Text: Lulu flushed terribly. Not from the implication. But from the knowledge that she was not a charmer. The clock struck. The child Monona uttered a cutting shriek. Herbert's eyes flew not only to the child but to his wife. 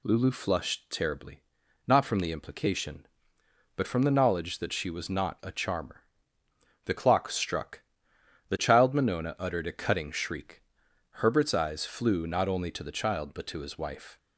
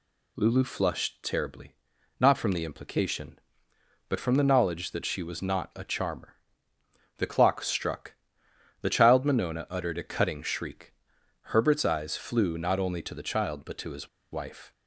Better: first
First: none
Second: pauses between "his" and "wife"; slight; at 14.0 s; 0.23 s long

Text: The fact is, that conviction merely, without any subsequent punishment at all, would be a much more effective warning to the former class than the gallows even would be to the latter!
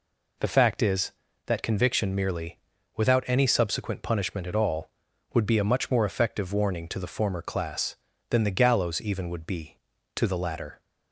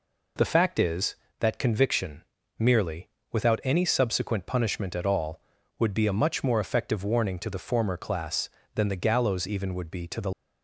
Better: first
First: none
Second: pauses between "conviction" and "merely"; slight; at 2.2 s; 0.36 s long // stops before "latter"; at 10.3 s

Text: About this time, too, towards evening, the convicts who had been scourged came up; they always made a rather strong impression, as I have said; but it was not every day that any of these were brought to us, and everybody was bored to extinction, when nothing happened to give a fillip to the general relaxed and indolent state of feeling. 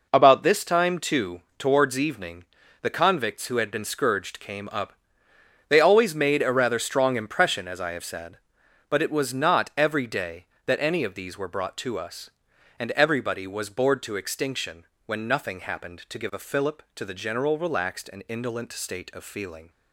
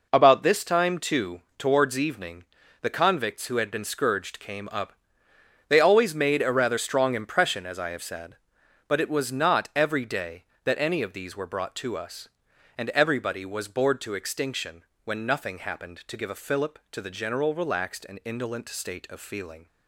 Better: neither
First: none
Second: none

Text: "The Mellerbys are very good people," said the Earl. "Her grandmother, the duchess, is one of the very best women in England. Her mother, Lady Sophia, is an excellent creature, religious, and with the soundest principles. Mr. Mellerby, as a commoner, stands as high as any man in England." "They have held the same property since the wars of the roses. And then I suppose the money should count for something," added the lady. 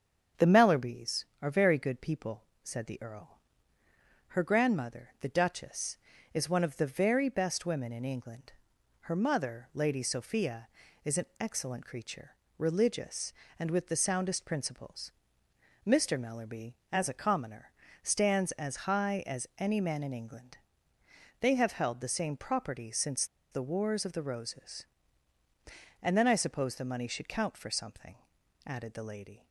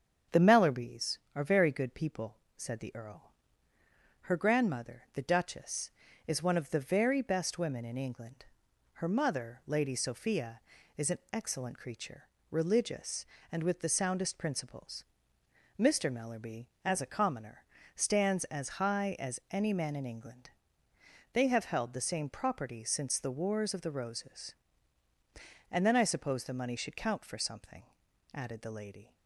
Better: second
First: starts louder than the rest; strong; until 1.5 s; 7.5 dB // pauses between "since" and "the"; slight; at 23.2 s; 0.26 s long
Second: starts louder than the rest; strong; until 1.4 s; 7.5 dB

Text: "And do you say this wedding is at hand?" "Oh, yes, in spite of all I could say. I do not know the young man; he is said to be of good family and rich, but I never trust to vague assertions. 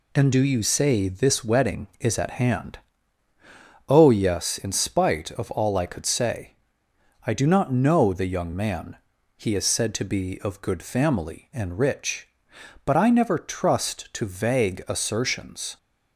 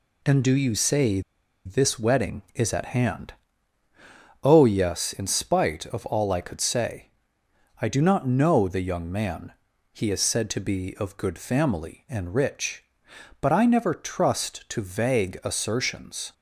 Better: first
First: none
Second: pauses between "say" and "this"; at 1.2 s; 0.45 s long

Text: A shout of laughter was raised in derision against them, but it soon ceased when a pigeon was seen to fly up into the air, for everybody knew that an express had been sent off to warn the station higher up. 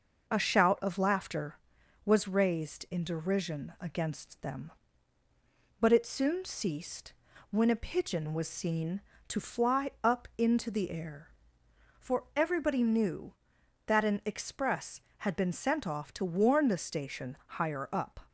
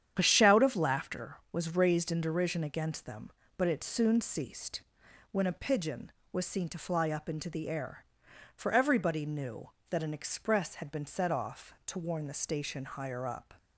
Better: first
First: pauses between "ceased" and "when"; at 7.1 s; 0.38 s long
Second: starts louder than the rest; strong; until 1.1 s; 9 dB // pauses between "ceased" and "when"; noticeable; at 4.8 s; 0.48 s long // says "set" for "sent"; at 11.0 s

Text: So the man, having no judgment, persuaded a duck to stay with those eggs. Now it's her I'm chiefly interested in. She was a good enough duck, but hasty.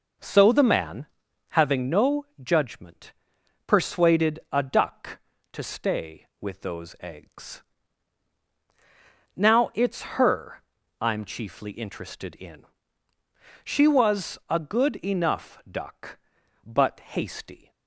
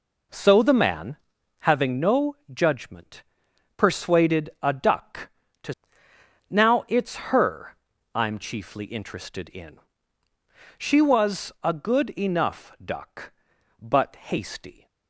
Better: first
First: pauses between "no" and "judgment"; slight; at 2.2 s; 0.16 s long // pauses between "her" and "I'm"; at 10.6 s; 0.38 s long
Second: pauses between "no" and "judgment"; slight; at 2.3 s; 0.16 s long // skips "stay with those eggs"; at 6.1 s // pauses between "her" and "I'm"; at 7.7 s; 0.38 s long

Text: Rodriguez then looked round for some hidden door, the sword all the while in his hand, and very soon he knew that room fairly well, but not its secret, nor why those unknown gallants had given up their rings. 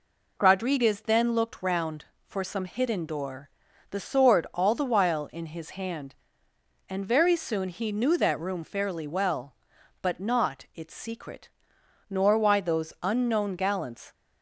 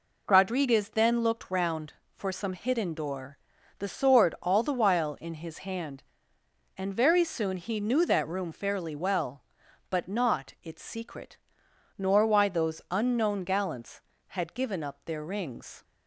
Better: second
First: stops before "had given up their rings"; at 14.1 s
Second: none

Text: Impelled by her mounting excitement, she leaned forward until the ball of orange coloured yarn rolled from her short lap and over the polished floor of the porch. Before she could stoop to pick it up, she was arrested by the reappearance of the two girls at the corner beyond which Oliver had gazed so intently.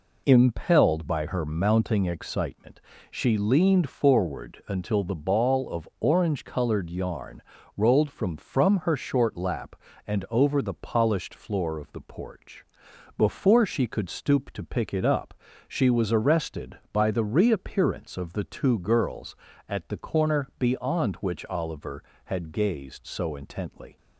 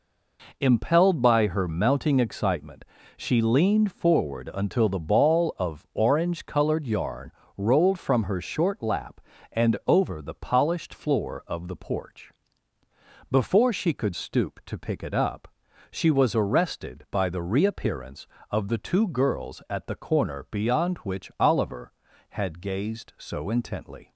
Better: second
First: pauses between "yarn" and "rolled"; slight; at 7.4 s; 0.34 s long // says "from" twice; at 8.3 s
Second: pauses between "yarn" and "rolled"; slight; at 7.3 s; 0.26 s long

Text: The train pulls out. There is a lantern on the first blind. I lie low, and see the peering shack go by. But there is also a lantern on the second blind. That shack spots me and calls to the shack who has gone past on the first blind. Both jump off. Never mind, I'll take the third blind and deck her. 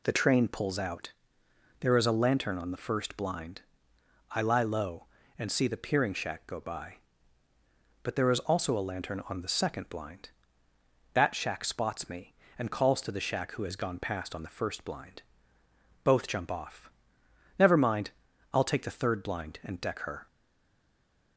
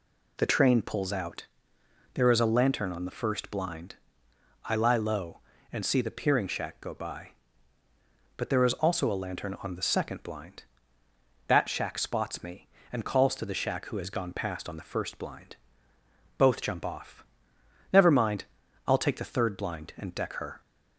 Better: second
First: stays silent after the last word; from 20.2 s on; 1.1 s long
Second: none

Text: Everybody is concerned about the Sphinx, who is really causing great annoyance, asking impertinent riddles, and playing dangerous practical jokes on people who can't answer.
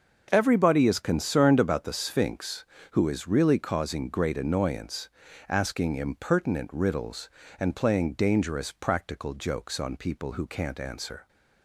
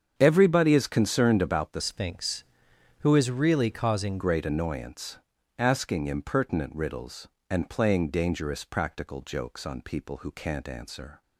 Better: first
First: starts louder than the rest; until 1.3 s; 6.5 dB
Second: starts louder than the rest; strong; until 1.1 s; 7.5 dB // changes voice from "Sphinx" to "causing"; from 1.8 to 4.1 s; 2.3 s long

